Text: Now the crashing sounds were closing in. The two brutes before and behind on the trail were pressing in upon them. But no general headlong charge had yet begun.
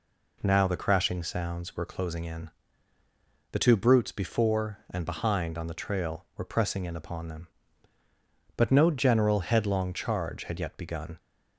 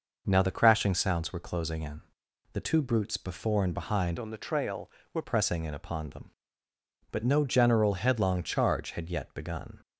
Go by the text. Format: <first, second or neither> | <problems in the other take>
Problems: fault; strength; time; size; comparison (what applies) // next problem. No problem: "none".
first | changes voice from "on" to "were"; from 4.1 to 5.2 s; 1.1 s long